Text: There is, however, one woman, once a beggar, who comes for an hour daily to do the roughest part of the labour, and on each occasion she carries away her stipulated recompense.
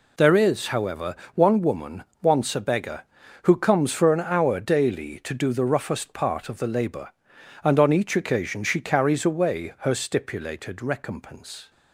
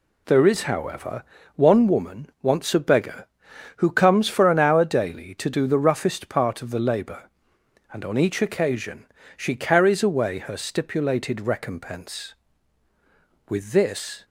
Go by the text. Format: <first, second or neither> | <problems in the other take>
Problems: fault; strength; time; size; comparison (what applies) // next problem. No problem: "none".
first | pauses between "occasion" and "she"; slight; at 9.0 s; 0.32 s long // goes on to say "With this"; noticeable; from 13.4 s on; 0.76 s long